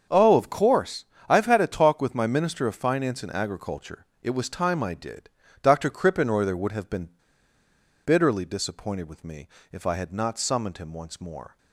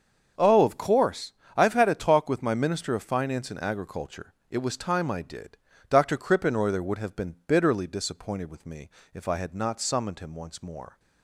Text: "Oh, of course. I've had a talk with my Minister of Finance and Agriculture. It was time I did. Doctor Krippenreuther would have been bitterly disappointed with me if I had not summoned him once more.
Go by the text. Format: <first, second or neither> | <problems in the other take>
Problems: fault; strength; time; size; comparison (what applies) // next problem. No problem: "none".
second | starts louder than the rest; until 1.3 s; 7 dB; strong in the second // pauses between "been" and "bitterly"; noticeable; at 7.0 s; 0.96 s long // pauses between "me" and "if"; slight; at 9.4 s; 0.24 s long; slight in the second